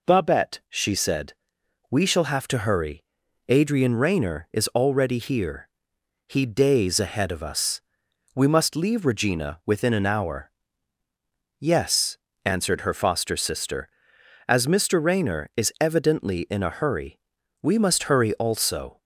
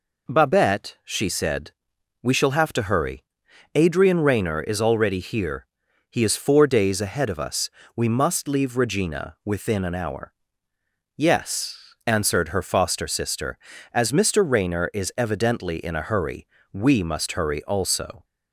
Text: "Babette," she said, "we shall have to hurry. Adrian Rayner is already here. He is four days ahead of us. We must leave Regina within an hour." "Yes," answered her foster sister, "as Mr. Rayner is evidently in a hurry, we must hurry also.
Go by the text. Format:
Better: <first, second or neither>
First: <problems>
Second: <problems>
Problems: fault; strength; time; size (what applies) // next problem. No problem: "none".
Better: second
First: skips "is four"; at 6.4 s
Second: none